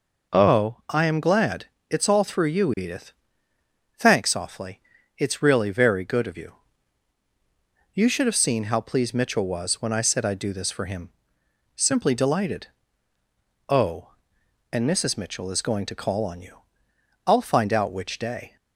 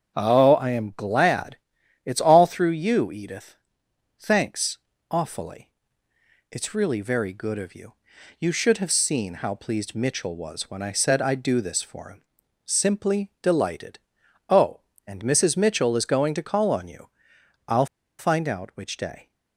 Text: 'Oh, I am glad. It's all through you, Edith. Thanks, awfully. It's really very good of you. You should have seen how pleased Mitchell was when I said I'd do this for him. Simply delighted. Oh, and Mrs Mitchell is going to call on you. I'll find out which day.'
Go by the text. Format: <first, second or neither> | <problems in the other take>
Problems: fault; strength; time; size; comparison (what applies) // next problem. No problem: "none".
first | starts louder than the rest; strong; until 1.2 s; 7.5 dB // pauses between "I'll" and "find"; slight; at 17.8 s; 0.33 s long